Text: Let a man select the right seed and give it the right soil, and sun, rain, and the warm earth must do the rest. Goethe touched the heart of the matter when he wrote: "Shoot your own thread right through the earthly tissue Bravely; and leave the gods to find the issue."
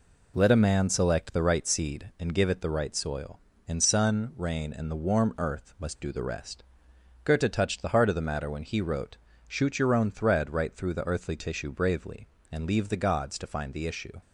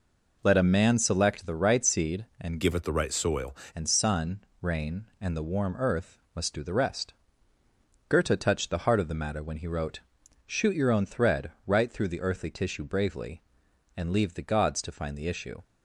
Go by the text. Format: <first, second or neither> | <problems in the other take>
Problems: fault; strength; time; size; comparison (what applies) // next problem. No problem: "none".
first | changes voice from "give" to "soil"; from 2.6 to 3.5 s; 0.9 s long // pauses between "earth" and "must"; slight; at 6.1 s; 0.18 s long // pauses between "thread" and "right"; slight; at 11.5 s; 0.16 s long